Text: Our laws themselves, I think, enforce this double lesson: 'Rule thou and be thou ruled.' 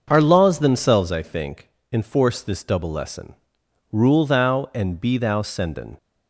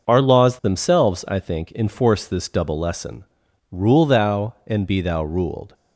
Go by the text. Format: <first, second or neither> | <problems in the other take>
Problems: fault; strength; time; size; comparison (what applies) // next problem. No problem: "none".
second | starts louder than the rest; noticeable; until 1.0 s; 6 dB // says "senden" for "ruled"; at 5.4 s